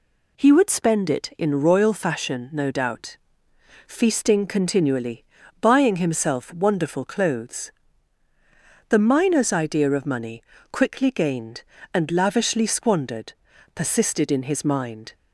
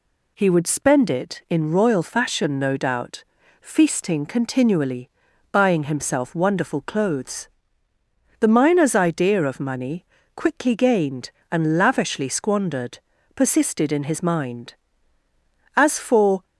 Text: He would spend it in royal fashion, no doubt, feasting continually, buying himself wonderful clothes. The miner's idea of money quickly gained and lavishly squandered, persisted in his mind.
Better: first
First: pauses between "money" and "quickly"; slight; at 10.4 s; 0.30 s long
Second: pauses between "money" and "quickly"; slight; at 10.0 s; 0.32 s long // goes on to say "As for"; noticeable; from 15.7 s on; 0.70 s long

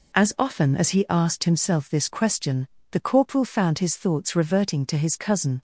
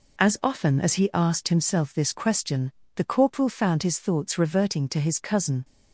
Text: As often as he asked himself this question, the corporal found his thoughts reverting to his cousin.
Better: neither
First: none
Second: none

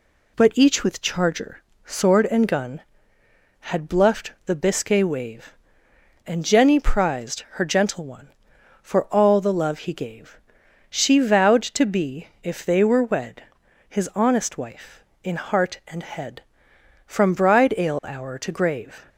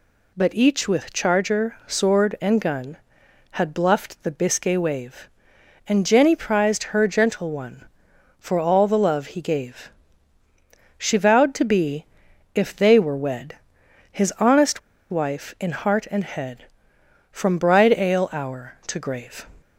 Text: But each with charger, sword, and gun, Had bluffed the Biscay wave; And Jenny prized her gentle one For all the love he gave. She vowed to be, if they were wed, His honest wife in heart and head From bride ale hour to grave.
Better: first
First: none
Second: pauses between "honest" and "wife"; slight; at 14.7 s; 0.31 s long

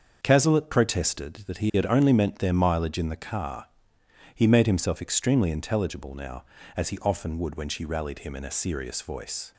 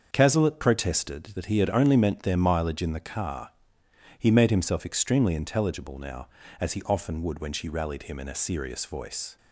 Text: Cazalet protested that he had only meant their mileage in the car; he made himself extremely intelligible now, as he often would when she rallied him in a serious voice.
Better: neither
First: starts louder than the rest; until 1.2 s; 6.5 dB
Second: starts louder than the rest; until 1.1 s; 6.5 dB

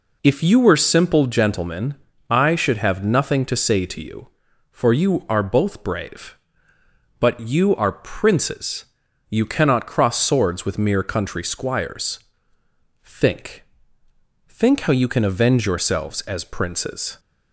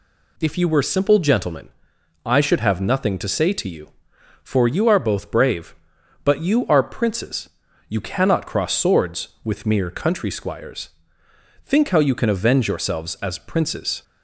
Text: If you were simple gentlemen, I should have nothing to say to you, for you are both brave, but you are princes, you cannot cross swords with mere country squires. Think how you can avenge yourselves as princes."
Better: second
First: says "Think" twice; at 14.4 s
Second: none

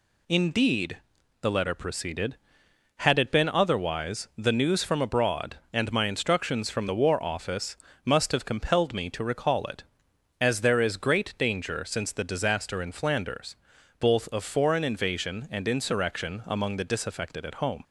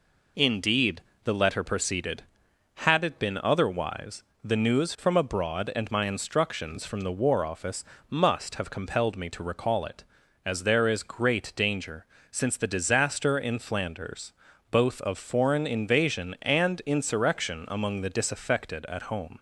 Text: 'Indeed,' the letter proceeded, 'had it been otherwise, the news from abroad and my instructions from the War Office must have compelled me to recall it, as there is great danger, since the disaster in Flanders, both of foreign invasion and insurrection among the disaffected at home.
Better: neither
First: pauses between "Office" and "must"; slight; at 7.7 s; 0.30 s long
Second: pauses between "Office" and "must"; slight; at 7.8 s; 0.26 s long

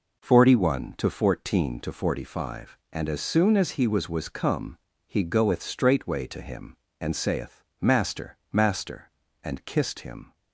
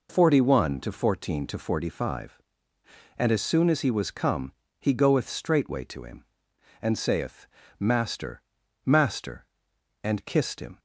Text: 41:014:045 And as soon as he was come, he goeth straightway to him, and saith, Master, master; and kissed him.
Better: second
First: says "was" twice; at 4.0 s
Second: none

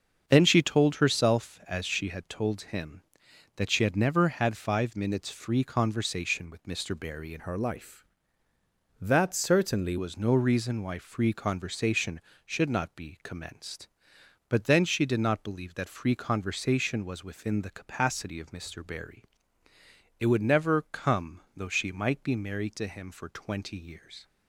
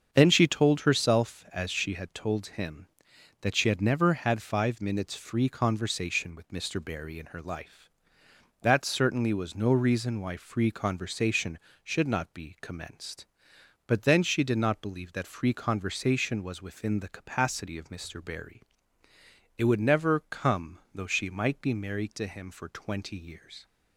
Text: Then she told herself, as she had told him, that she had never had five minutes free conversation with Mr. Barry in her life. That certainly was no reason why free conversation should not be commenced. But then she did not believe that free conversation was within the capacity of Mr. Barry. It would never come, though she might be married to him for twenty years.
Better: second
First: starts louder than the rest; until 1.2 s; 7 dB // changes voice from "her" to "certainly"; from 7.3 to 9.9 s; 2.6 s long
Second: starts louder than the rest; until 1.1 s; 7 dB

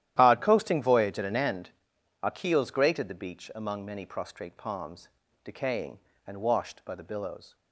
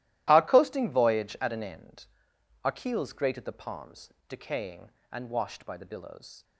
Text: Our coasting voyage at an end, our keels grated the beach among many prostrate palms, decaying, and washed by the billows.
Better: first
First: starts louder than the rest; strong; until 1.1 s; 12 dB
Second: starts louder than the rest; strong; until 1.2 s; 14.5 dB // skips "beach among many prostrate"; at 3.5 s

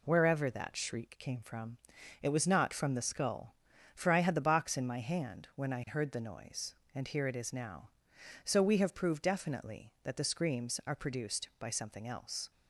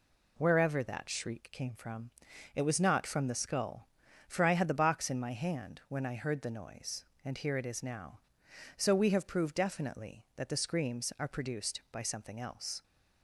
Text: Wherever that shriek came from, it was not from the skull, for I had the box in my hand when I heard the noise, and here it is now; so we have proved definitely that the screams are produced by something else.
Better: neither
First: none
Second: none

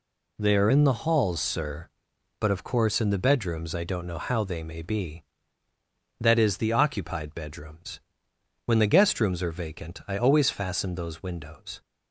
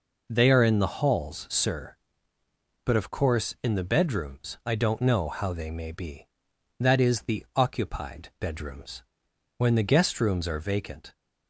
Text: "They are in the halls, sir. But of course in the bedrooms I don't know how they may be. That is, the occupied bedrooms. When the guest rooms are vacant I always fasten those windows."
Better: first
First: none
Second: stops before "I always fasten those windows"; at 11.1 s

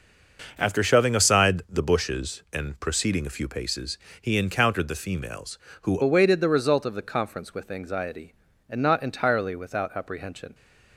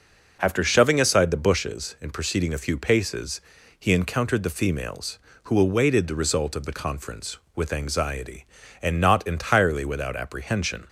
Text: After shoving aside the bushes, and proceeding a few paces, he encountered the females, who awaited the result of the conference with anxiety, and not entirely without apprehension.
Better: second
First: changes voice at "awaited"; from 6.0 s on; 4.5 s long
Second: none

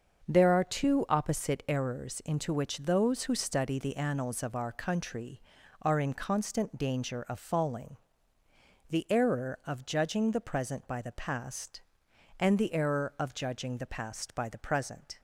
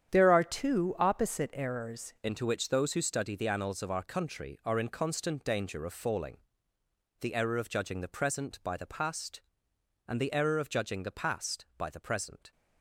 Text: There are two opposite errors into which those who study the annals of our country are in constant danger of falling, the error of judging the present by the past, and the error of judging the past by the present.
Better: first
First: starts louder than the rest; until 1.3 s; 7 dB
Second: starts louder than the rest; strong; until 1.1 s; 9 dB // changes voice at "into"; from 2.2 s on; 10.3 s long

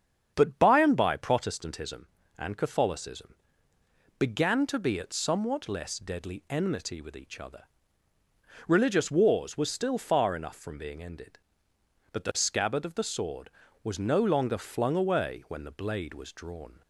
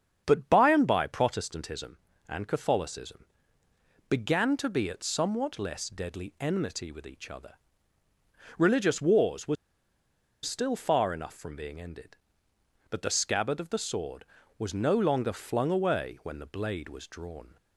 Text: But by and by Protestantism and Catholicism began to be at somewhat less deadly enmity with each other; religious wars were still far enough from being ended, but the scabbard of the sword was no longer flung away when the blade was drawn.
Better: first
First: starts louder than the rest; strong; until 1.3 s; 7.5 dB // pauses between "Catholicism" and "began"; noticeable; at 3.3 s; 0.84 s long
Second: starts louder than the rest; strong; until 1.2 s; 7.5 dB // pauses between "Catholicism" and "began"; noticeable; at 3.2 s; 0.84 s long // pauses between "were" and "still"; noticeable; at 9.5 s; 0.88 s long

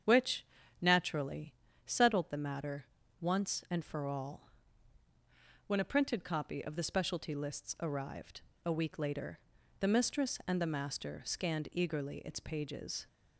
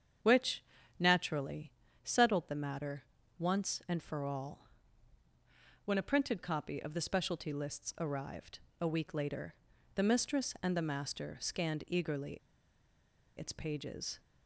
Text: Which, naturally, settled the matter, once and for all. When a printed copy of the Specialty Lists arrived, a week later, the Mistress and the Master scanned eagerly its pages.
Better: first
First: starts louder than the rest; strong; until 1.4 s; 8 dB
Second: starts louder than the rest; strong; until 1.6 s; 8 dB // pauses between "eagerly" and "its"; at 12.3 s; 0.99 s long

